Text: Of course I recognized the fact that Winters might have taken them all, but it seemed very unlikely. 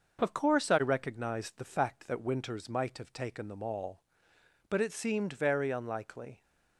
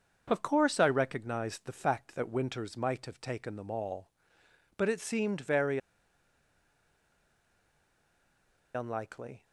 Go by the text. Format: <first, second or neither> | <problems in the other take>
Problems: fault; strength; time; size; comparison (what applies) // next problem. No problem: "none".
first | starts louder than the rest; until 1.2 s; 6.5 dB; noticeable in the first // pauses between "very" and "unlikely"; strong; at 5.7 s; 2.9 s long